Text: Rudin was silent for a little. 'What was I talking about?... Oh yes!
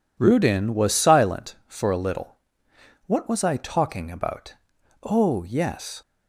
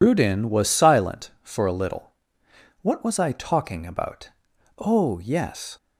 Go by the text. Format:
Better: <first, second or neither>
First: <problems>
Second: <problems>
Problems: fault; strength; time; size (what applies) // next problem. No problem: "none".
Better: first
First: none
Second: loses the start of "Rudin"; at 0.0 s; 70 ms